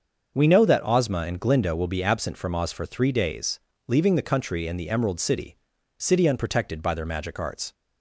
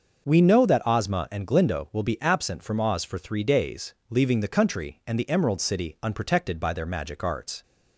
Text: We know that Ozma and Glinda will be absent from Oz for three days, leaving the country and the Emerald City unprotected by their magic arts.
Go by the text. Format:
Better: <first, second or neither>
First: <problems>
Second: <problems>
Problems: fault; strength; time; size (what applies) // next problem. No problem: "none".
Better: second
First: starts louder than the rest; until 1.3 s; 6.5 dB // says "City" twice; at 5.9 s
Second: starts louder than the rest; until 1.2 s; 6 dB